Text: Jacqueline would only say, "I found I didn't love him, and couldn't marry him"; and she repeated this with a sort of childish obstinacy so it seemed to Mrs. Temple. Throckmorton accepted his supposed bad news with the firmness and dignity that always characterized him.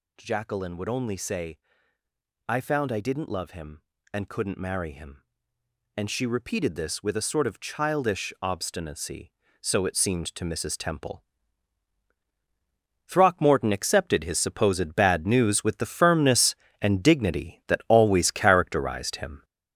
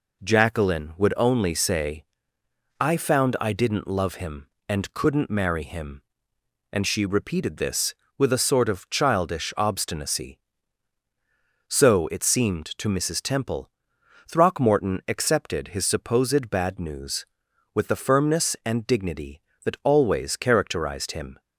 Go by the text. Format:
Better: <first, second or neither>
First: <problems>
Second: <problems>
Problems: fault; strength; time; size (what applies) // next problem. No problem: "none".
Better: second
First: gets louder; noticeable; throughout; 6 dB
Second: none